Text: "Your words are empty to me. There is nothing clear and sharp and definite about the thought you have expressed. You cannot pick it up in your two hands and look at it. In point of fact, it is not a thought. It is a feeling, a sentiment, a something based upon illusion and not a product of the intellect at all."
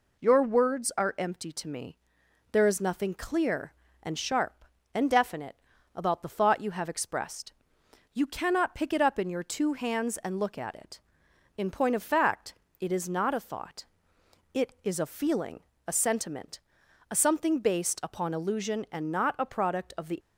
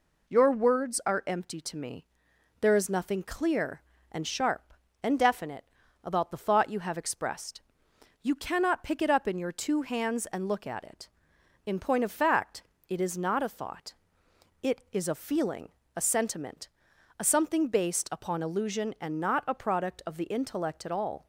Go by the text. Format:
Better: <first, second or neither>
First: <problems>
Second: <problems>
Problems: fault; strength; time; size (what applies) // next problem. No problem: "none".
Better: second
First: pauses between "definite" and "about"; at 5.5 s; 0.38 s long // stops before "intellect at all"; at 20.1 s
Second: pauses between "definite" and "about"; at 5.6 s; 0.38 s long